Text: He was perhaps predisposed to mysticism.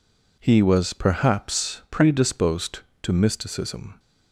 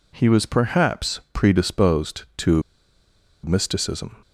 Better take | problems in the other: first | pauses between "to" and "mysticism"; noticeable; at 2.6 s; 0.81 s long

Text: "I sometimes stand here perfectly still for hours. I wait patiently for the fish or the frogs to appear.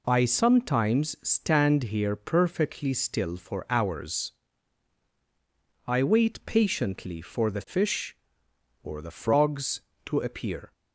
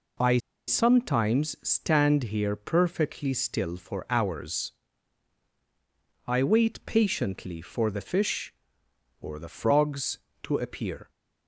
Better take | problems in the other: first | pauses between "I" and "sometimes"; slight; at 0.3 s; 0.29 s long

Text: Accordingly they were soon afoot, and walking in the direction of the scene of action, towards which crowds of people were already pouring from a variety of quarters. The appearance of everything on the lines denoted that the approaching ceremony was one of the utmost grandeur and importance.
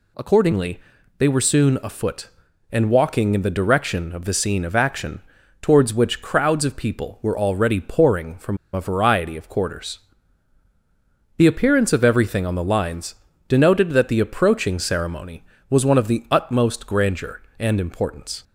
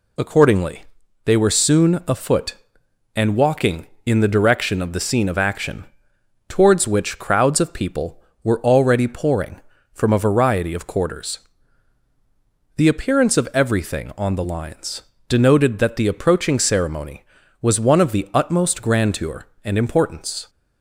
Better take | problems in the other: second | pauses between "Accordingly" and "they"; at 0.7 s; 0.40 s long; also in the second // pauses between "from" and "a"; slight; at 8.5 s; 0.16 s long // pauses between "lines" and "denoted"; slight; at 13.1 s; 0.32 s long; slight in the second

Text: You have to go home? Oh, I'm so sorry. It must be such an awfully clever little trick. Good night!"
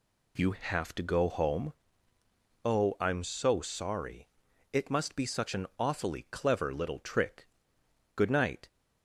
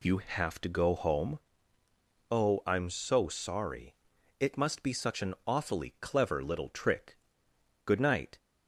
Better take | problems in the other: neither | none

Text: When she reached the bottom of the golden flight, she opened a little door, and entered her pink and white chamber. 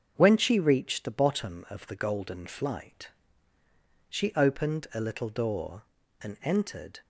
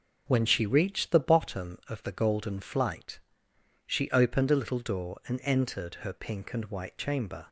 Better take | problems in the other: second | starts louder than the rest; until 1.1 s; 7 dB // stops before "her pink and white chamber"; at 7.0 s

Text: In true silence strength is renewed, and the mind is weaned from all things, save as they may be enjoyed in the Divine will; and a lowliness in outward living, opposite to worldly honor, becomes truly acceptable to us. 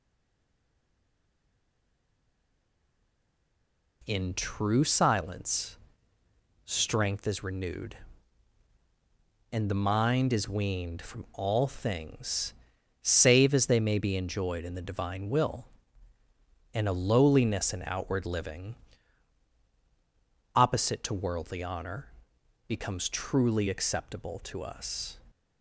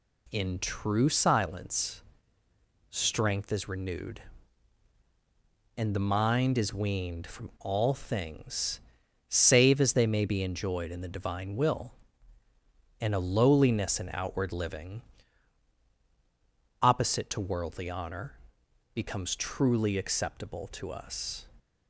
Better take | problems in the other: second | stays silent before the first word; strong; until 4.0 s; 4.0 s long // pauses between "silence" and "strength"; noticeable; at 5.7 s; 0.88 s long; noticeable in the second

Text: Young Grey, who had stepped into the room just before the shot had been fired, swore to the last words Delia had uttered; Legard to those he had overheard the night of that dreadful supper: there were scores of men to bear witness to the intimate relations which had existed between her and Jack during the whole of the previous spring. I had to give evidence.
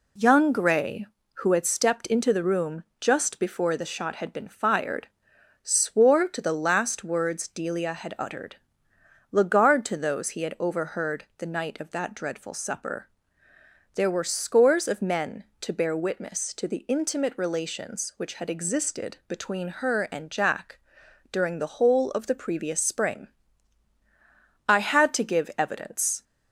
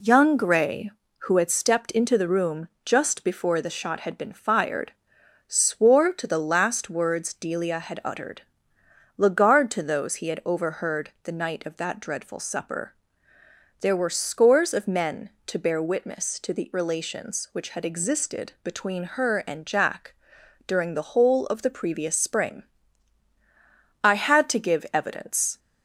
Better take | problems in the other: first | pauses between "room" and "just"; slight; at 2.6 s; 0.16 s long; slight in the first // skips "intimate"; at 16.7 s // pauses between "Jack" and "during"; noticeable; at 20.1 s; 0.56 s long; noticeable in the first

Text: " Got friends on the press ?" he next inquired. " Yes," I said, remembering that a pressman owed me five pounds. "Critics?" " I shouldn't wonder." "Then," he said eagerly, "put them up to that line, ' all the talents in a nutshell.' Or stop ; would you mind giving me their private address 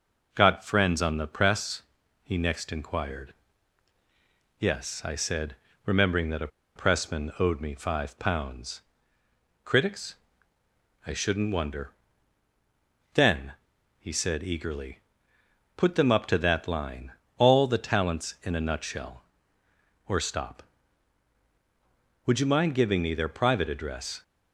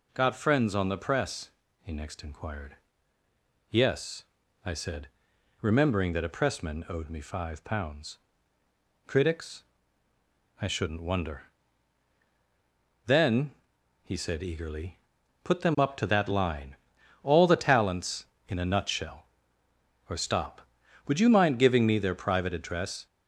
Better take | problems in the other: second | starts louder than the rest; noticeable; until 1.3 s; 6 dB // pauses between "a" and "pressman"; slight; at 6.4 s; 0.27 s long

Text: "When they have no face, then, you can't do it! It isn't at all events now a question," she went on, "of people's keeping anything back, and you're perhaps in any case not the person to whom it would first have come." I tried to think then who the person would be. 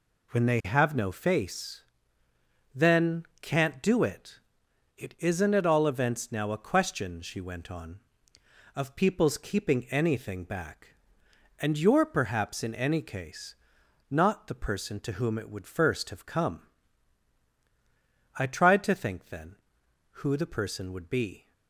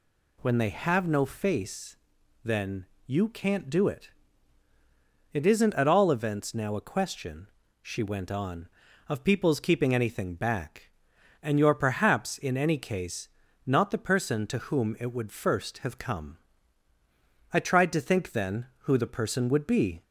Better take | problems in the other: second | skips "you"; at 3.3 s // pauses between "case" and "not"; noticeable; at 13.5 s; 0.54 s long; also in the second

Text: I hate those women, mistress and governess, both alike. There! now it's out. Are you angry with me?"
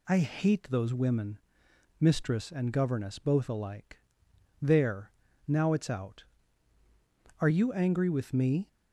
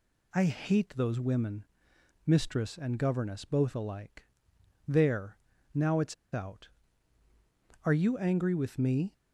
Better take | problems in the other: first | pauses between "it's" and "out"; slight; at 6.1 s; 0.17 s long

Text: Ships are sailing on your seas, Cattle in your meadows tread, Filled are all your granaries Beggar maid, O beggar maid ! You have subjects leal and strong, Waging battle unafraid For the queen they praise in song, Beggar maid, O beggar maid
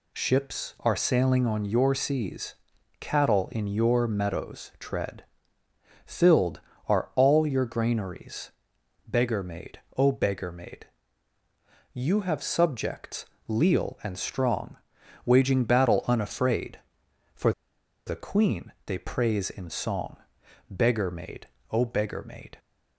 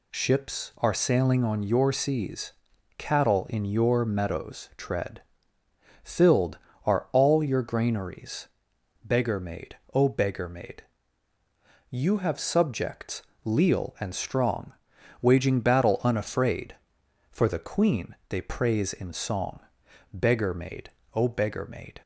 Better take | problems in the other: second | pauses between "granaries" and "Beggar"; noticeable; at 8.5 s; 0.56 s long; noticeable in the second // pauses between "subjects" and "leal"; slight; at 13.2 s; 0.22 s long; slight in the second // pauses between "For" and "the"; noticeable; at 17.5 s; 0.56 s long

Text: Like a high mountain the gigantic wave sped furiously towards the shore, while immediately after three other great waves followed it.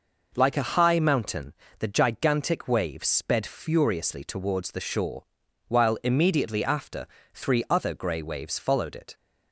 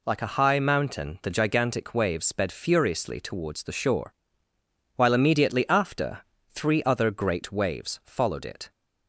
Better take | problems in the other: second | pauses between "mountain" and "the"; slight; at 1.5 s; 0.24 s long // pauses between "after" and "three"; slight; at 7.0 s; 0.30 s long; slight in the second // says "grey" for "great"; at 7.9 s

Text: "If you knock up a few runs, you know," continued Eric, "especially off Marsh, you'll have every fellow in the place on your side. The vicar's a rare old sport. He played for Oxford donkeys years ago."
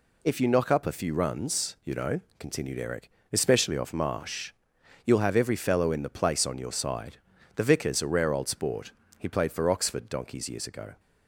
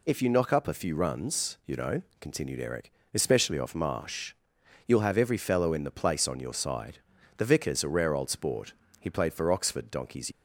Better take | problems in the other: first | stops before "years ago"; at 10.3 s

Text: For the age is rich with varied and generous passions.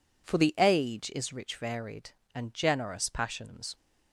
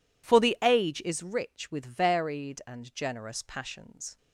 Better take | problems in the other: second | skips "with"; at 1.5 s

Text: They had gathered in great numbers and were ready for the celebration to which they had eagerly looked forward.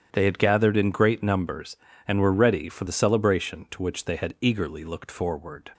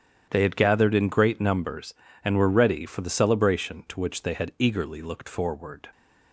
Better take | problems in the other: neither | starts louder than the rest; strong; the same in both

